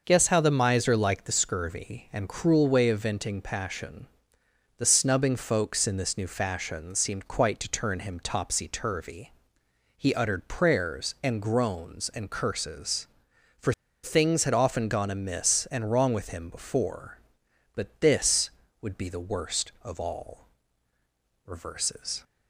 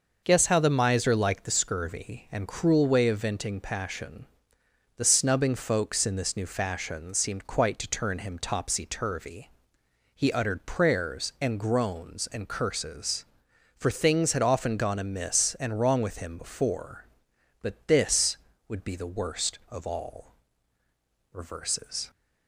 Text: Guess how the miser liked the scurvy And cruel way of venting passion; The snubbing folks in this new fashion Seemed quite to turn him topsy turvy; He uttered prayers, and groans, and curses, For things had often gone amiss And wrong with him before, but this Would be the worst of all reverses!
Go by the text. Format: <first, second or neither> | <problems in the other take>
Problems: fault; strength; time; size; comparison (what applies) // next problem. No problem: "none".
second | pauses between "For" and "things"; slight; at 13.7 s; 0.31 s long // pauses between "all" and "reverses"; noticeable; at 20.4 s; 0.98 s long; noticeable in the second